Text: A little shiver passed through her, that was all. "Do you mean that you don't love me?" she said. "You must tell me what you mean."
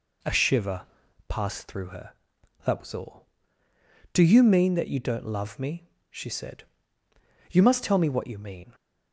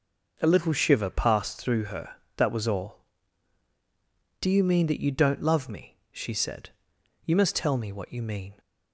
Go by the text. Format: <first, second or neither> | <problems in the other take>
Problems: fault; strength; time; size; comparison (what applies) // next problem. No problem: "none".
second | skips "little"; at 0.3 s // pauses between "shiver" and "passed"; noticeable; at 0.8 s; 0.46 s long